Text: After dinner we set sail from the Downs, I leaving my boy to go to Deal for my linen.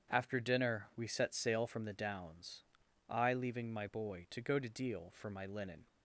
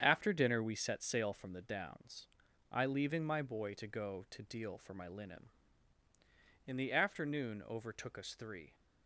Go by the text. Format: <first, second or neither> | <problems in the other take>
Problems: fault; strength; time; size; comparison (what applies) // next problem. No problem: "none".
first | starts louder than the rest; strong; until 1.0 s; 8 dB; strong in the first // goes on to say "In the afternoon overtook us three"; strong; from 6.6 s on; 2.0 s long